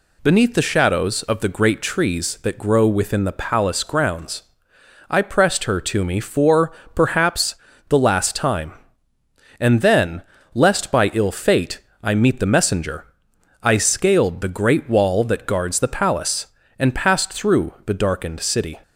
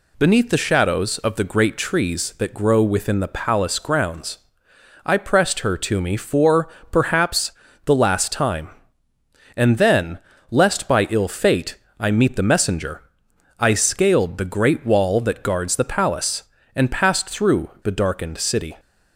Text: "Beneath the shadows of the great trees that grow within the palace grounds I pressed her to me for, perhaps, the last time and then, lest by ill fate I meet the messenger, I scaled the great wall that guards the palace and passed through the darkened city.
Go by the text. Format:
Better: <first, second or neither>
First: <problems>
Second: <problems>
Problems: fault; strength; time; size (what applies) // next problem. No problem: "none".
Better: neither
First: pauses between "grounds" and "I"; noticeable; at 4.4 s; 0.68 s long // pauses between "fate" and "I"; slight; at 11.7 s; 0.24 s long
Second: pauses between "grounds" and "I"; noticeable; at 4.3 s; 0.68 s long // pauses between "fate" and "I"; slight; at 11.7 s; 0.24 s long